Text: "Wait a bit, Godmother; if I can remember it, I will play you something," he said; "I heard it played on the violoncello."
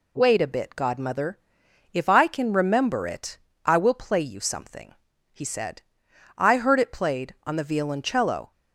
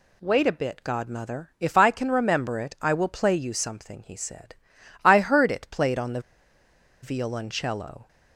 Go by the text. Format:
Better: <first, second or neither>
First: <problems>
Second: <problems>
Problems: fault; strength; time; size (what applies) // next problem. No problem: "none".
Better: first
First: none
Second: pauses between "the" and "violoncello"; noticeable; at 6.1 s; 0.83 s long